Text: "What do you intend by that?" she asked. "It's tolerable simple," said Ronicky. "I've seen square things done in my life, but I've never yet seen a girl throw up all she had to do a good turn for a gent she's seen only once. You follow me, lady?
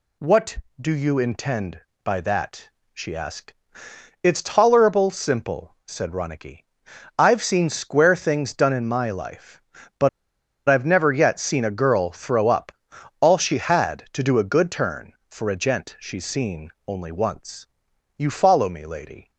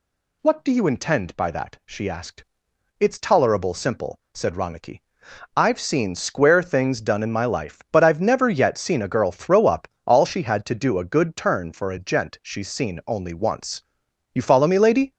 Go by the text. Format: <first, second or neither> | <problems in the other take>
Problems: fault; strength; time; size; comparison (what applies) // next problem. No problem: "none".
second | pauses between "but" and "I've"; noticeable; at 10.0 s; 0.58 s long // pauses between "up" and "all"; noticeable; at 12.7 s; 0.50 s long; slight in the second // pauses between "seen" and "only"; slight; at 16.6 s; 0.16 s long